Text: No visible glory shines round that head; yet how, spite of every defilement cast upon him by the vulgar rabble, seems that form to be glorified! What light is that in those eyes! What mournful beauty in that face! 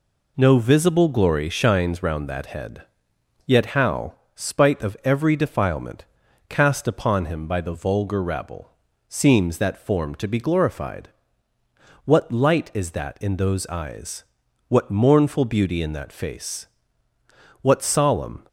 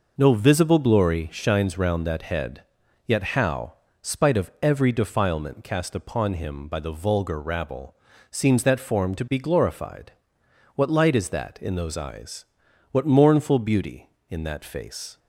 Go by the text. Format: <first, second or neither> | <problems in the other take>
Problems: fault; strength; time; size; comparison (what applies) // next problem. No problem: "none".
second | pauses between "defilement" and "cast"; at 6.0 s; 0.42 s long // goes on to say "What solemn"; noticeable; from 17.6 s on; 0.84 s long